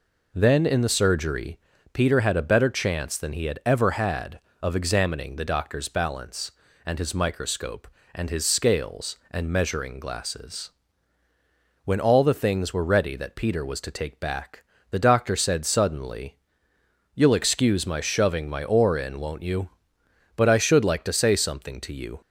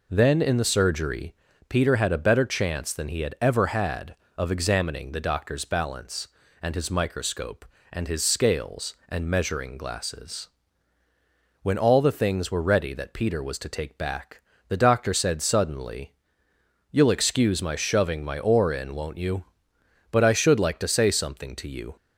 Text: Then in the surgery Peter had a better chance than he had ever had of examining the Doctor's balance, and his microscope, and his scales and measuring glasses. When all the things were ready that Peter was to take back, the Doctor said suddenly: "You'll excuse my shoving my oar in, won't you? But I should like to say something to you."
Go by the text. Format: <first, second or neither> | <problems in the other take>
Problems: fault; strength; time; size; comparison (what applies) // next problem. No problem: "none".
neither | pauses between "surgery" and "Peter"; slight; the same in both